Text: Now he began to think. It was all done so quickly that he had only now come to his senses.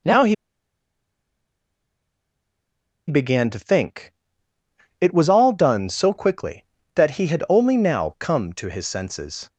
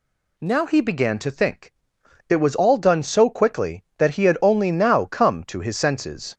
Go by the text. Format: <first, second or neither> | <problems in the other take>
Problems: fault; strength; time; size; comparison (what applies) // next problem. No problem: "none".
second | pauses between "he" and "began"; strong; at 0.3 s; 2.7 s long